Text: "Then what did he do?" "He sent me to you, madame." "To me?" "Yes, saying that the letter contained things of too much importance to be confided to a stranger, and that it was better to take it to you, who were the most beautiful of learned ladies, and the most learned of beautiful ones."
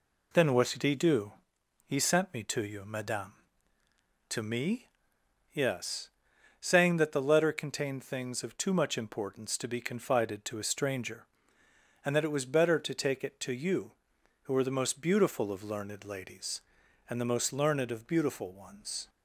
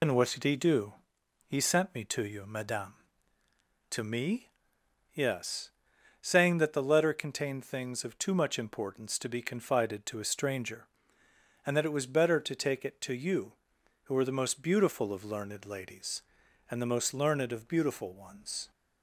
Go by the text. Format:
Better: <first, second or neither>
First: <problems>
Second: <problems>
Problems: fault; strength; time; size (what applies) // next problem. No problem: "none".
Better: first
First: none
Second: loses the start of "Then"; at 0.0 s; 80 ms